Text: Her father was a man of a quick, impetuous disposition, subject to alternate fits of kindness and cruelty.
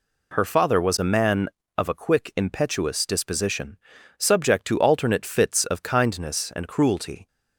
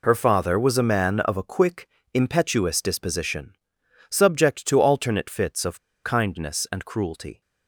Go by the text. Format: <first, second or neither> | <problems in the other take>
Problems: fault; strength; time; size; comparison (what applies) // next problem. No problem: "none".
first | pauses between "of" and "kindness"; slight; at 5.7 s; 0.24 s long